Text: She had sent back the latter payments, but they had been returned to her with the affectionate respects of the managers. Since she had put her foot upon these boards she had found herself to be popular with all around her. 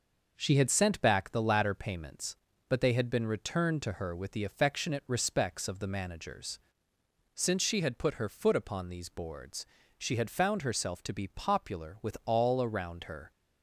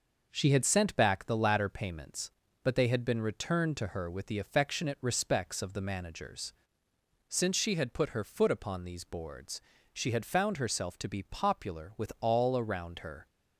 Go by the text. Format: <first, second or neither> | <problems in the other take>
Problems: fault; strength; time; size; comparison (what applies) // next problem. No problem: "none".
neither | pauses between "boards" and "she"; slight; the same in both